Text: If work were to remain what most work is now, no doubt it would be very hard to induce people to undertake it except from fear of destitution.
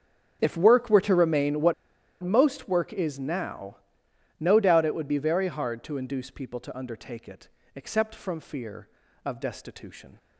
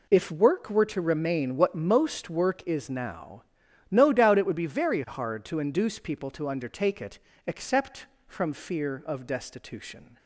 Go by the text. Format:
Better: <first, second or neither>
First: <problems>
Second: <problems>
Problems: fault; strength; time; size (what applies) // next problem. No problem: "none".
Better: second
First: starts louder than the rest; strong; until 1.4 s; 7.5 dB // pauses between "what" and "most"; noticeable; at 1.7 s; 0.49 s long // pauses between "it" and "except"; slight; at 7.4 s; 0.26 s long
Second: pauses between "it" and "except"; slight; at 7.1 s; 0.26 s long